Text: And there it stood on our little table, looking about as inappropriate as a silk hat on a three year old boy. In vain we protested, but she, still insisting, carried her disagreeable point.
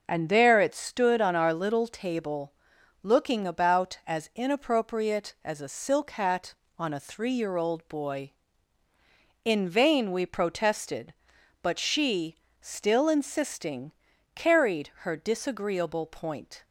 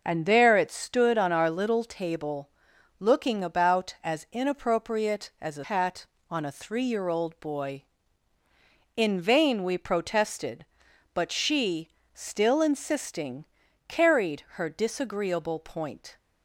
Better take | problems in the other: first | skips "silk"; at 5.6 s

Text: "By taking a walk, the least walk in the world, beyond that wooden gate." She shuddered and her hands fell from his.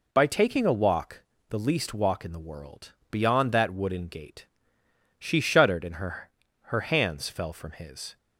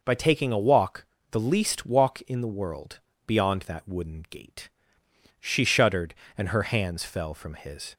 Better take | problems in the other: second | says "her" twice; at 6.6 s

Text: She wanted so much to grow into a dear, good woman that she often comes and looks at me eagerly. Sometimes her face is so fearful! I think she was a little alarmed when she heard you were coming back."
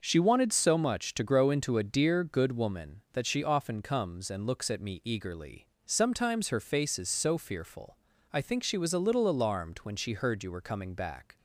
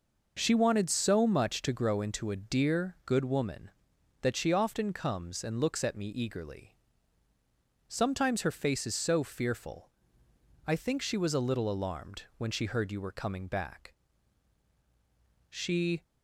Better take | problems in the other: first | goes on to say "She"; from 15.4 s on; 0.54 s long

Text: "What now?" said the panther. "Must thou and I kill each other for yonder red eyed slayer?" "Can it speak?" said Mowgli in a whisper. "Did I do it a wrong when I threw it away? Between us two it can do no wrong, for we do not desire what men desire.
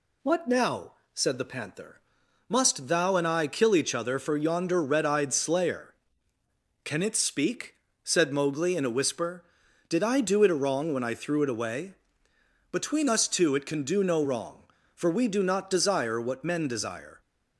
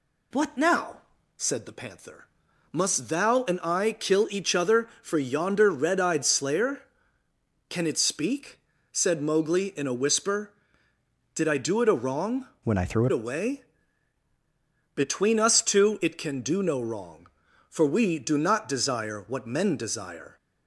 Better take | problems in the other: first | changes voice from "when" to "it"; from 12.6 to 13.1 s; 0.5 s long

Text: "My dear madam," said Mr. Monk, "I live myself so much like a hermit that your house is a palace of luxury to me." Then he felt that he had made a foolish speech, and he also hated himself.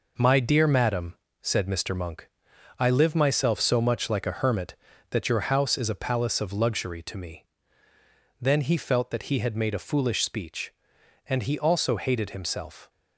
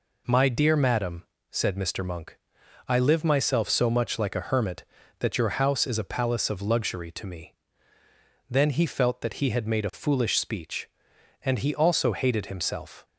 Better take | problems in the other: second | gets quieter; throughout; 6.5 dB

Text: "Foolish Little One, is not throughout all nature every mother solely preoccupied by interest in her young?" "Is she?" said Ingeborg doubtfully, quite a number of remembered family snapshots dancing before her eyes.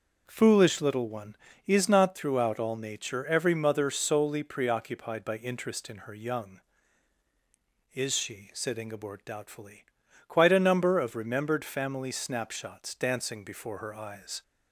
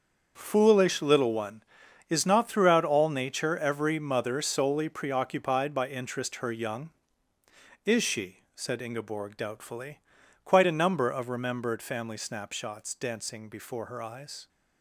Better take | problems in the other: first | starts louder than the rest; until 1.3 s; 6.5 dB // skips "in"; at 6.3 s

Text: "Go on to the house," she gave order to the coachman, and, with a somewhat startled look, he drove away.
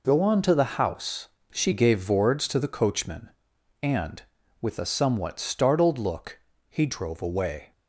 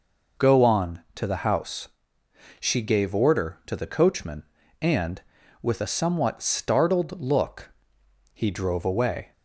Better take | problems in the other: second | says "vords" for "order"; at 1.9 s

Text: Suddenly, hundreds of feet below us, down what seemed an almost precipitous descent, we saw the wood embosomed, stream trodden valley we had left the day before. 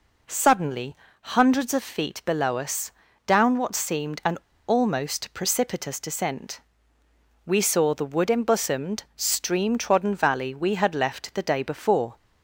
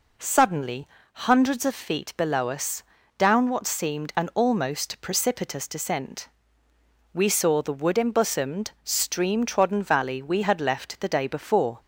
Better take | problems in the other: second | pauses between "an" and "almost"; slight; at 4.3 s; 0.30 s long

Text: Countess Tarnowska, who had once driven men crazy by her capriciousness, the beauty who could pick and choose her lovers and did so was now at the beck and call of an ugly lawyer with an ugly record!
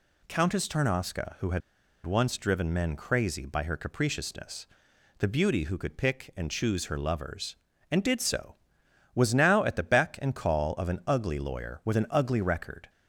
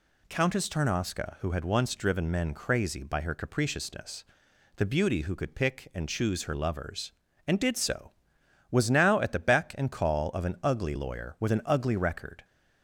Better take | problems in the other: second | pauses between "had" and "once"; at 1.6 s; 0.44 s long

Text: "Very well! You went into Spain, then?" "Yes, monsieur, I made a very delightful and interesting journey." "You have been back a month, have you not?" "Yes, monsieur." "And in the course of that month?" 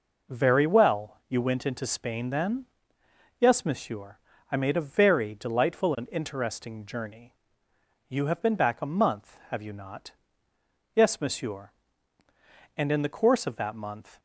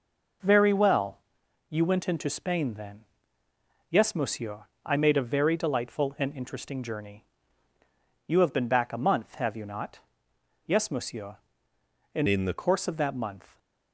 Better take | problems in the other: first | changes voice from "in" to "the"; from 12.2 to 12.5 s; 0.3 s long

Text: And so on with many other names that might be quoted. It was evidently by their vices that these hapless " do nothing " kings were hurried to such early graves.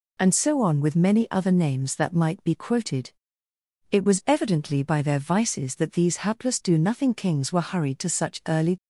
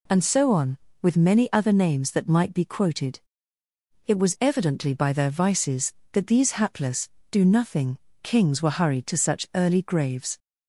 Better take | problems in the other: second | stops before "graves"; at 8.7 s

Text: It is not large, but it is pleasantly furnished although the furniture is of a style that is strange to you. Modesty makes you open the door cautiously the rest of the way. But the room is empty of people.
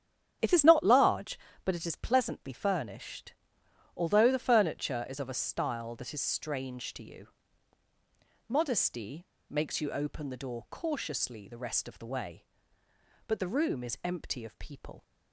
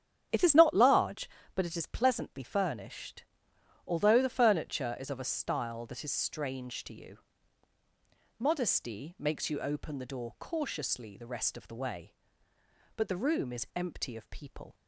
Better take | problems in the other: second | starts louder than the rest; strong; until 1.6 s; 9.5 dB; strong in the second // pauses between "furnished" and "although"; noticeable; at 3.3 s; 0.64 s long; noticeable in the second // pauses between "Modesty" and "makes"; slight; at 9.2 s; 0.25 s long

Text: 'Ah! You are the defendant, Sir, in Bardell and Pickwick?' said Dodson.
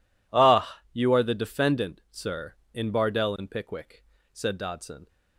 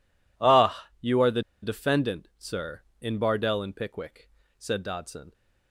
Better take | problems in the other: first | pauses between "the" and "defendant"; slight; at 1.4 s; 0.20 s long

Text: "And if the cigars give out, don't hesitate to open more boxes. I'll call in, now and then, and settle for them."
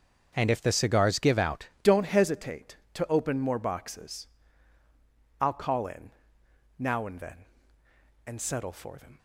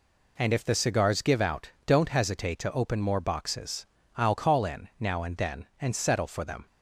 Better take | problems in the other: second | starts louder than the rest; until 1.3 s; 6.5 dB // changes voice at "don't"; from 1.8 s on; 7.3 s long

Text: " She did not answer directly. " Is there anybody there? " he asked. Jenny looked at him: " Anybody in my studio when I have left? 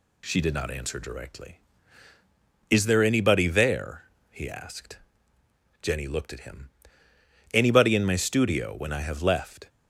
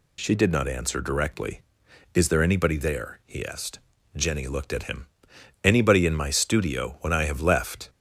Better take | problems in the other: neither | none

